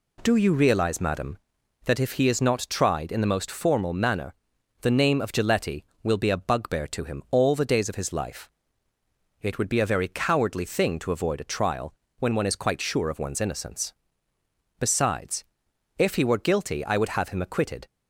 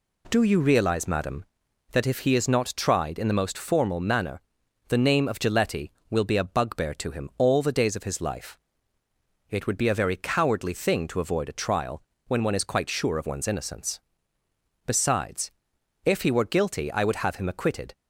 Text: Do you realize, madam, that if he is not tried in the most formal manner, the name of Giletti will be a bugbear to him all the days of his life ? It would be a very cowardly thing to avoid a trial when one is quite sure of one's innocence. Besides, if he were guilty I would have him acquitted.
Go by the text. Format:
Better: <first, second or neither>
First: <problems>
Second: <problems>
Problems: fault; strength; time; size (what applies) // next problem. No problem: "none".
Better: neither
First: pauses between "trial" and "when"; slight; at 11.9 s; 0.24 s long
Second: pauses between "trial" and "when"; slight; at 12.0 s; 0.24 s long